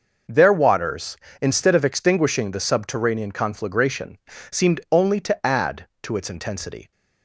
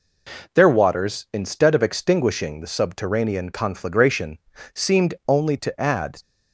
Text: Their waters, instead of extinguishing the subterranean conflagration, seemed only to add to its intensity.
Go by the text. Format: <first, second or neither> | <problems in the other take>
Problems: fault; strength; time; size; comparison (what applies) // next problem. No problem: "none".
first | stops before "to its intensity"; at 6.2 s